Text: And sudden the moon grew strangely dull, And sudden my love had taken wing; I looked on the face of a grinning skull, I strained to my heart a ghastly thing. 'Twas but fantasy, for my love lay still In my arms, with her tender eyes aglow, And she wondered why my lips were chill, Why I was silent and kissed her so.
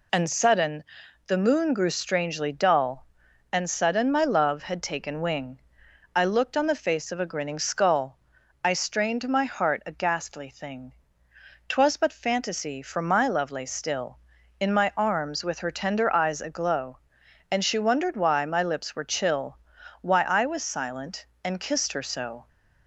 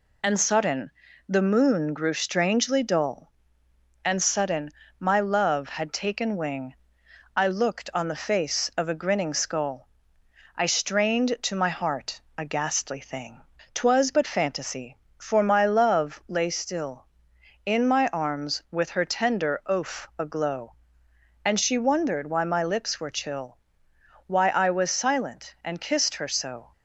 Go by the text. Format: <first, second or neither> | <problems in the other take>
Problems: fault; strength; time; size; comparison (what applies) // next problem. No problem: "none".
first | pauses between "sudden" and "the"; at 0.8 s; 0.38 s long; noticeable in the first // pauses between "sudden" and "my"; slight; at 4.7 s; 0.26 s long // pauses between "heart" and "a"; slight; at 12.1 s; 0.16 s long // says "oaf" for "eyes"; at 19.6 s